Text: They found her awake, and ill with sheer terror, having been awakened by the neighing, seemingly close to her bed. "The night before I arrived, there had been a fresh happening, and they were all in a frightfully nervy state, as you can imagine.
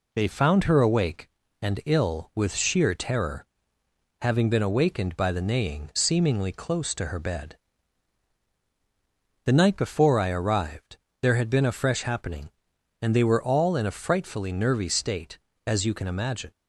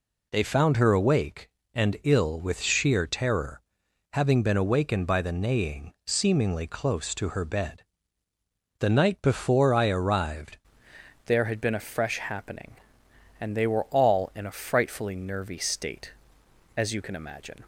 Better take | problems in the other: first | changes voice at "there"; from 11.2 s on; 6.4 s long

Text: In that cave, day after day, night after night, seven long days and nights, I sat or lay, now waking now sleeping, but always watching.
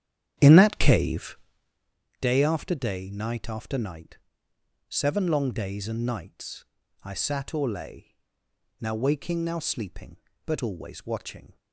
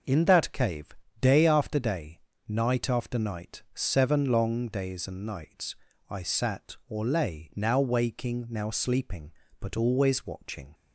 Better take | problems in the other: second | starts louder than the rest; strong; until 1.7 s; 9.5 dB

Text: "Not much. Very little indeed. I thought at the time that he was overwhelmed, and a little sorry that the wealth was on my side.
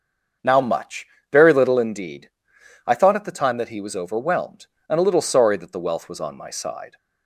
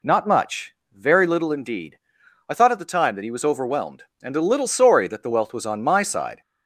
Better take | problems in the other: second | starts louder than the rest; until 1.6 s; 6.5 dB // says "Now" for "Not"; at 0.4 s

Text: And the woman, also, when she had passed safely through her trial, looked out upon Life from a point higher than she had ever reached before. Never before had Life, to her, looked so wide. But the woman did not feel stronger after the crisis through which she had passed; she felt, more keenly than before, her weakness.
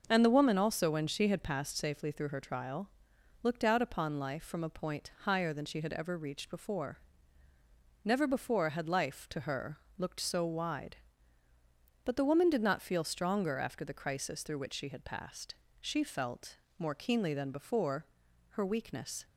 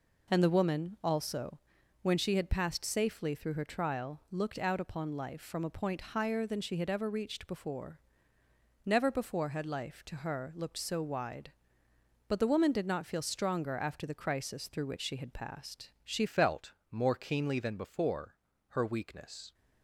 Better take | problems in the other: first | changes voice at "felt"; from 16.2 s on; 3.3 s long

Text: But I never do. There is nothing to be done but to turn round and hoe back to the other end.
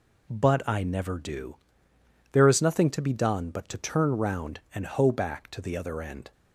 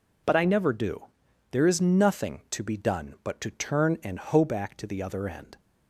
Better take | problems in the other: first | skips "round"; at 4.0 s

